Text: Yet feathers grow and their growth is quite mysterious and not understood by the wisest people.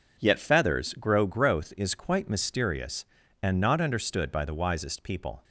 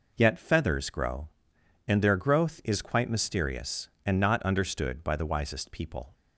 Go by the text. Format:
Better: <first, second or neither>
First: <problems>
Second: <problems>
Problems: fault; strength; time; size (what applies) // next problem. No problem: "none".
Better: second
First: skips "and their"; at 1.2 s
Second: none